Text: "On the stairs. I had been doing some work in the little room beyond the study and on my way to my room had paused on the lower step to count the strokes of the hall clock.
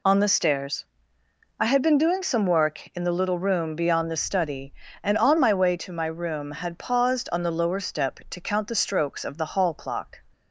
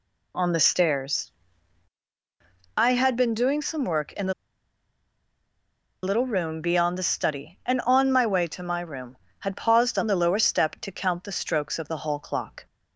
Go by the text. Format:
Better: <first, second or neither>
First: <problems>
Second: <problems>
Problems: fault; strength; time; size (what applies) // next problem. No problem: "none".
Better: first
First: none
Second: pauses between "the" and "little"; strong; at 4.3 s; 1.7 s long